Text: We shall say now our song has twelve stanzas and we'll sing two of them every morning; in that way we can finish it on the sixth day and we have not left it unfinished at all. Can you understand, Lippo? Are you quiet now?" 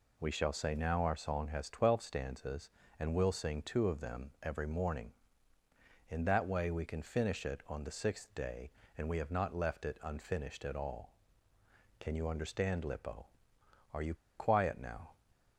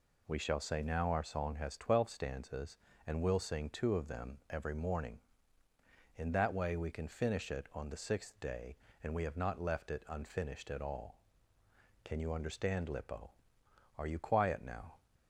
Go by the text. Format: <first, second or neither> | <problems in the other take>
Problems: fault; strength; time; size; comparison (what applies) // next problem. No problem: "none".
second | pauses between "you" and "quiet"; slight; at 14.1 s; 0.22 s long